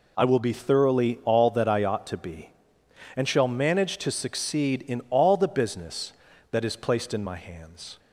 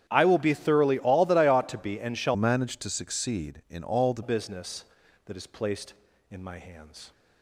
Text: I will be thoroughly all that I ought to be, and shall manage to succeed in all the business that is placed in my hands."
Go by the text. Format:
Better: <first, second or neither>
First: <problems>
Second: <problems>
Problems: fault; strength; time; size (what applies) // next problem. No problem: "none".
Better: first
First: none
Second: starts louder than the rest; strong; until 1.0 s; 9.5 dB // changes voice from "manage" to "the"; from 2.3 to 4.2 s; 1.9 s long